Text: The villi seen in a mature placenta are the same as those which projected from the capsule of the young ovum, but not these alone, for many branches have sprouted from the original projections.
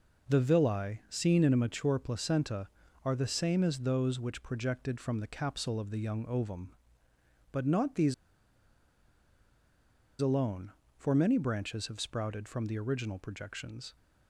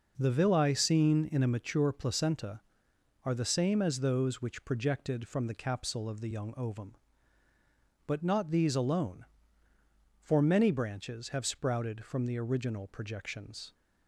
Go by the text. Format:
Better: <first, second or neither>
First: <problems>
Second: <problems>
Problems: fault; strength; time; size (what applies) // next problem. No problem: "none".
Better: second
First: pauses between "these" and "alone"; strong; at 8.1 s; 2.0 s long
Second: none